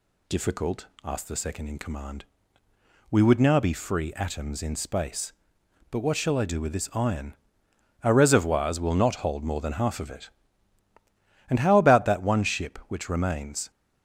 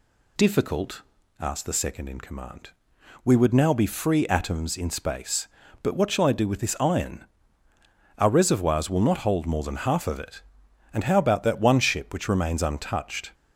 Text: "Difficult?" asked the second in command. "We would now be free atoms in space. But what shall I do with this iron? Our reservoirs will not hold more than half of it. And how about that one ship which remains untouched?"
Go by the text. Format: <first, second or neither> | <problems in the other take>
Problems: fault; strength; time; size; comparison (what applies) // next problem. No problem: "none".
second | stops before "untouched"; at 13.7 s